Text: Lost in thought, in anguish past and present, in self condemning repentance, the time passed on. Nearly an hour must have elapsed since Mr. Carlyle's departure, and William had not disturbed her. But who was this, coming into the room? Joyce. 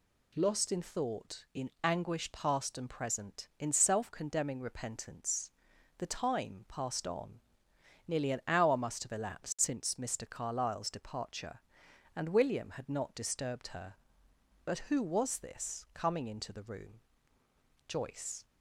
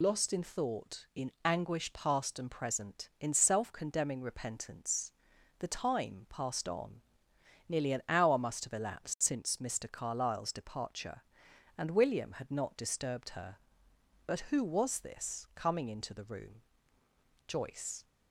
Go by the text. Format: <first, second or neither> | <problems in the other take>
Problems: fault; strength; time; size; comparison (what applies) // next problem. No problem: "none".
first | loses the start of "Lost"; at 0.0 s; 70 ms